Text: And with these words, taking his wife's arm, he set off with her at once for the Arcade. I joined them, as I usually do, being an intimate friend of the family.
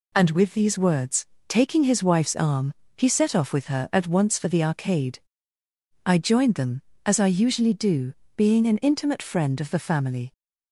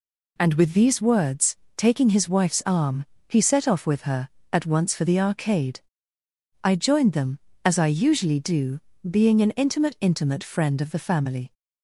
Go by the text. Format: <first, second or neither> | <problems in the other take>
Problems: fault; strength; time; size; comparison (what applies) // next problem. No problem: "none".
first | says "intimate" twice; at 10.0 s